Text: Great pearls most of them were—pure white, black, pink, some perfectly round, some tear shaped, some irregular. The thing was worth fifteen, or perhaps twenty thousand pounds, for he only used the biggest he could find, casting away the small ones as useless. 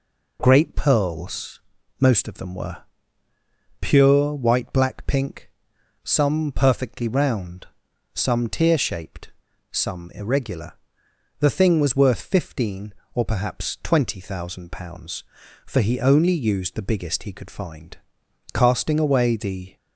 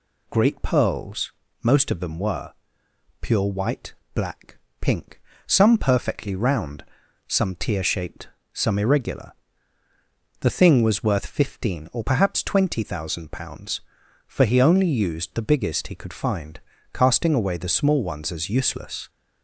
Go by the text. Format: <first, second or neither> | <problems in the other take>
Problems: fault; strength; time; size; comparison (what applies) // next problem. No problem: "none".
second | pauses between "pearls" and "most"; at 1.6 s; 0.38 s long; slight in the second // stops before "small ones as useless"; at 19.7 s